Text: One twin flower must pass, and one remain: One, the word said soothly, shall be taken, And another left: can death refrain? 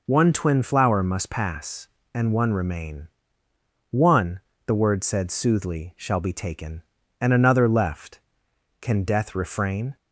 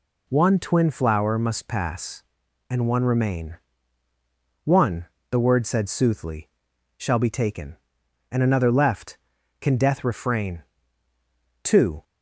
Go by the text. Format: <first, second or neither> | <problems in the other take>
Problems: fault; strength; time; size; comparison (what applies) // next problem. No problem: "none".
first | goes on to say "Two"; slight; from 11.6 s on; 0.40 s long